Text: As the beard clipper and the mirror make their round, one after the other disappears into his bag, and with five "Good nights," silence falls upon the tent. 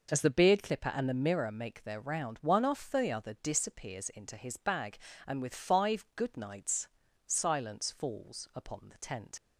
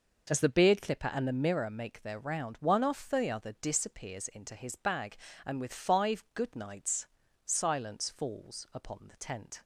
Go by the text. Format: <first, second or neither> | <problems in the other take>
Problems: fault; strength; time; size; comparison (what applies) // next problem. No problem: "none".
second | leaves "tent" unfinished; at 9.3 s; 55 ms